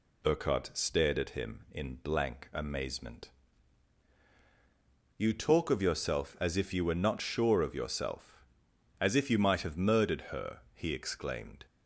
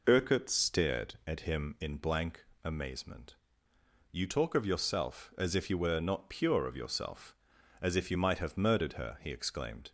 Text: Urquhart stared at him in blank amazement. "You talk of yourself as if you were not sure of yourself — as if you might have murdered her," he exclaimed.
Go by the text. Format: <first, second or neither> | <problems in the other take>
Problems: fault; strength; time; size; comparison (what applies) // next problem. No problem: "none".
first | pauses between "blank" and "amazement"; slight; at 2.4 s; 0.18 s long // says "pure" for "sure"; at 6.2 s